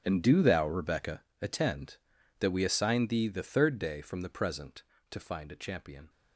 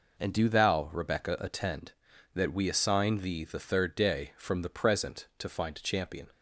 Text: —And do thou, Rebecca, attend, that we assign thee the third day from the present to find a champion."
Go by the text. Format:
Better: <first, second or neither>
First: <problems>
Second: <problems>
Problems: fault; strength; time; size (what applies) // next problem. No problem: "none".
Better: second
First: gets quieter; strong; throughout; 16.5 dB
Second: none